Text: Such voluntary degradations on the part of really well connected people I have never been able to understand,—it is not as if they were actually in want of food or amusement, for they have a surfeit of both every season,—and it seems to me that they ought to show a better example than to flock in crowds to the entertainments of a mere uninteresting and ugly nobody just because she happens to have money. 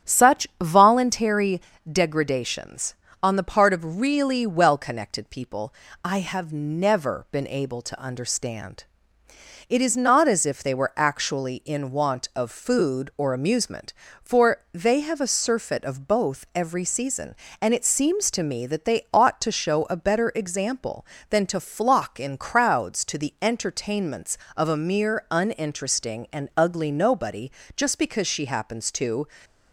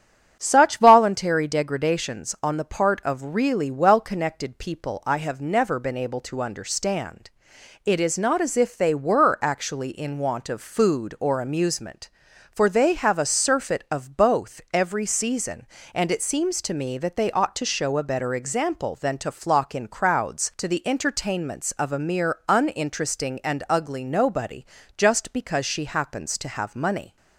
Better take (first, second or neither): second